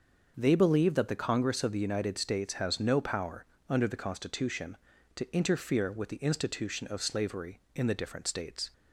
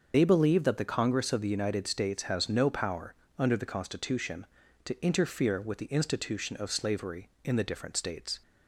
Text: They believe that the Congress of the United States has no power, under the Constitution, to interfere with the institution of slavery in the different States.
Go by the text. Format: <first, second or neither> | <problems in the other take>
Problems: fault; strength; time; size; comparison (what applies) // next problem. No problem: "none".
first | loses the start of "They"; at 0.1 s; 90 ms // starts louder than the rest; until 1.1 s; 6.5 dB; also in the first